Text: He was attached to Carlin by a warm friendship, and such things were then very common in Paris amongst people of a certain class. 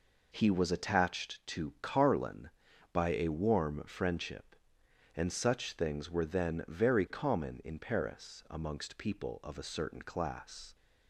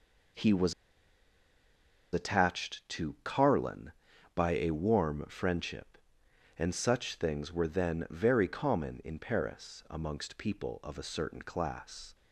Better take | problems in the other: first | pauses between "was" and "attached"; strong; at 0.7 s; 1.3 s long

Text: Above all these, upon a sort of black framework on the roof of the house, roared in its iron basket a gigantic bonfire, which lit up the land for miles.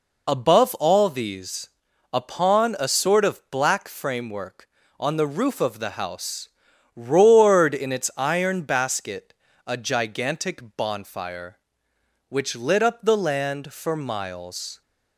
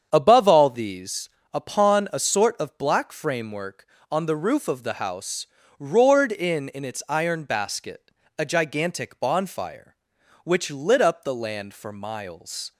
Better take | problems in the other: first | starts louder than the rest; strong; until 1.1 s; 7.5 dB // says "in" twice; at 6.6 s // pauses between "basket" and "a"; slight; at 8.1 s; 0.26 s long; slight in the first

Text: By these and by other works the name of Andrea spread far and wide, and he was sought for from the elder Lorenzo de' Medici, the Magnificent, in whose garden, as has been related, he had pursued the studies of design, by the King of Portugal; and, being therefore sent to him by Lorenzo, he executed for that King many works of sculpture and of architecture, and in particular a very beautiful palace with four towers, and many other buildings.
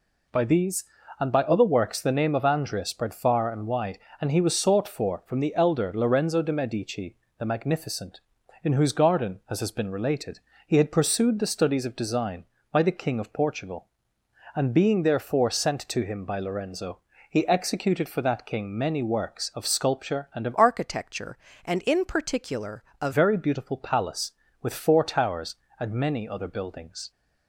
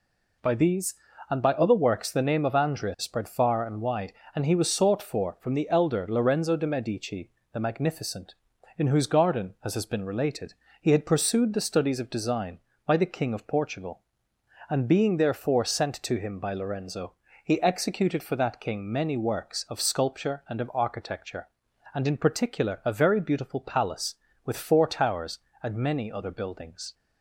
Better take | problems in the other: second | changes voice from "architecture" to "a"; from 20.5 to 23.1 s; 2.6 s long // pauses between "particular" and "a"; slight; at 22.8 s; 0.16 s long

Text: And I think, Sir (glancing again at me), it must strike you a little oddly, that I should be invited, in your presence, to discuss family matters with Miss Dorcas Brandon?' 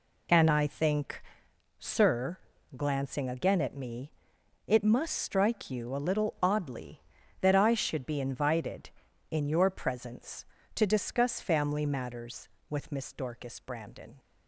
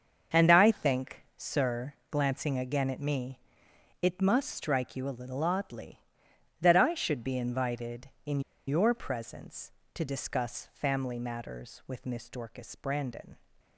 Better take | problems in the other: first | starts louder than the rest; until 1.4 s; 6.5 dB // pauses between "in" and "your"; slight; at 8.4 s; 0.27 s long

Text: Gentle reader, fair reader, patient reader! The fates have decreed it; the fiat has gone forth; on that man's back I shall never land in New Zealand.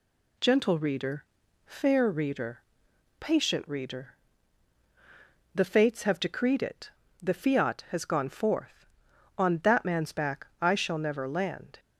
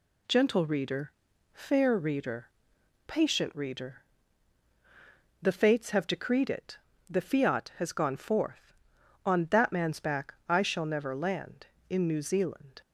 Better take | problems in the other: second | pauses between "back" and "I"; slight; at 10.4 s; 0.16 s long; slight in the second // stops before "in New Zealand"; at 11.7 s

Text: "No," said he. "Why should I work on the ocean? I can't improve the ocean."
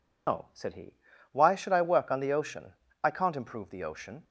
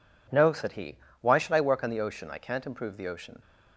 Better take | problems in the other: second | loses the start of "No"; at 0.2 s; 140 ms

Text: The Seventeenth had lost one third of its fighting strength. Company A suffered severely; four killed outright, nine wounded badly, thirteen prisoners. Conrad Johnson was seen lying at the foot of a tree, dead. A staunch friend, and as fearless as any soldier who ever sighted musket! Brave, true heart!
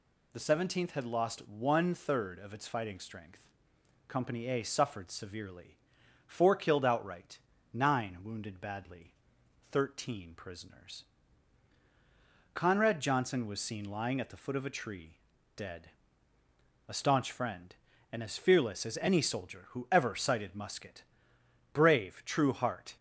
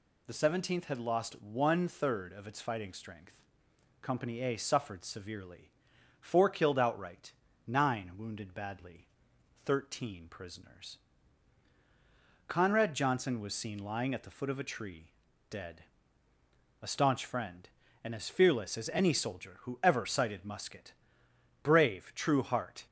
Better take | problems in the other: neither | none

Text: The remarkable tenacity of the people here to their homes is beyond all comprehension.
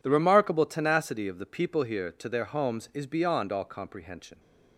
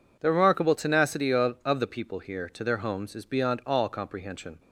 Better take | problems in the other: first | says "of" twice; at 1.6 s

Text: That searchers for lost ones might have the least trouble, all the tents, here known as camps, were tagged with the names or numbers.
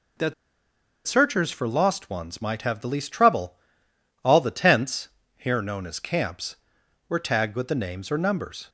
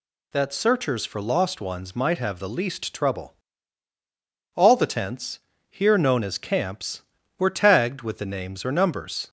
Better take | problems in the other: second | pauses between "That" and "searchers"; noticeable; at 0.3 s; 0.72 s long

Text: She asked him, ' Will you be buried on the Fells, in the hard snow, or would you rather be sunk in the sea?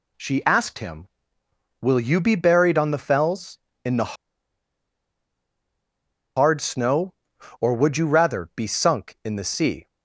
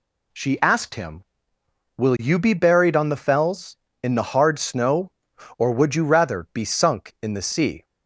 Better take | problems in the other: second | pauses between "the" and "hard"; strong; at 4.1 s; 2.2 s long

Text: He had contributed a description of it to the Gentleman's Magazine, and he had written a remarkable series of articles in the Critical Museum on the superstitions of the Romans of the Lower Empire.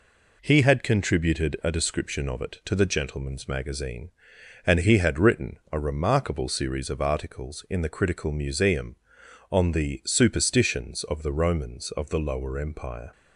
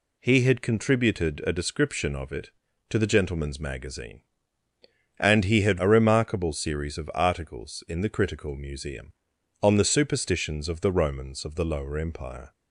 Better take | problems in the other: first | skips "written"; at 5.7 s

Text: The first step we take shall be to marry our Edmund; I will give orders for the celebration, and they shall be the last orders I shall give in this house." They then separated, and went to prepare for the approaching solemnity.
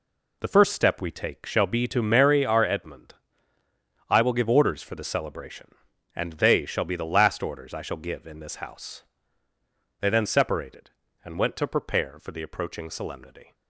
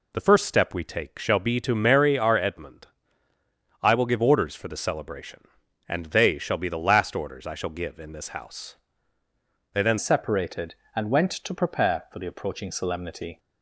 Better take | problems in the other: first | changes voice at "separated"; from 9.9 s on; 3.4 s long

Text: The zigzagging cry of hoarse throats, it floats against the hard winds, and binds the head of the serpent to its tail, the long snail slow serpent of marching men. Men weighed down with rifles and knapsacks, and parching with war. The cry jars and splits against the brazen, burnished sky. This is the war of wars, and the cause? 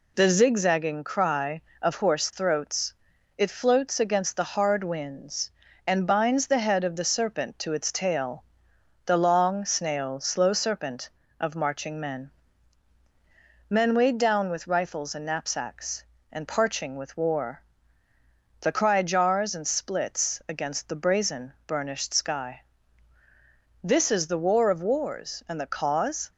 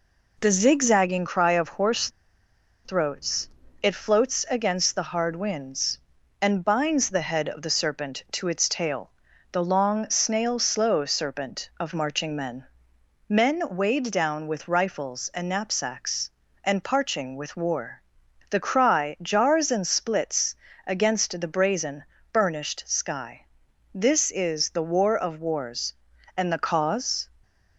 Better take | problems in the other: first | pauses between "hoarse" and "throats"; noticeable; at 2.1 s; 0.74 s long // pauses between "splits" and "against"; slight; at 20.5 s; 0.30 s long

